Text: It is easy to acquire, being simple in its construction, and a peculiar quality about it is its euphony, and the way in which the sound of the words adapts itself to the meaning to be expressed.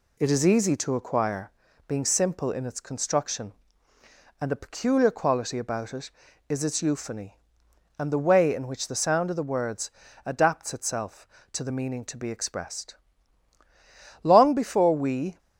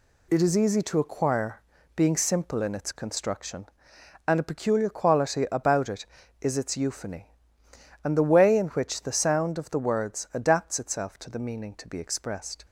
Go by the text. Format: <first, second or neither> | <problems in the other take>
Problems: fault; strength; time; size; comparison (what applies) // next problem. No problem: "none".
second | pauses between "words" and "adapts"; slight; at 9.9 s; 0.34 s long // goes on to say "Long before we"; noticeable; from 14.2 s on; 1.1 s long